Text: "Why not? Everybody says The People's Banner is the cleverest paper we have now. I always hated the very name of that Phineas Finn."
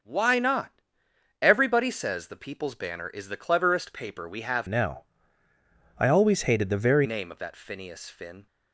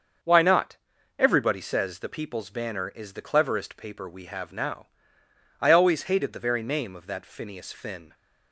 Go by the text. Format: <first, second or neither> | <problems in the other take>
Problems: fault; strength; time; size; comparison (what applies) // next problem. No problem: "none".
second | starts louder than the rest; noticeable; until 1.6 s; 6 dB; also in the second // changes voice from "now" to "very"; from 4.6 to 7.0 s; 2.4 s long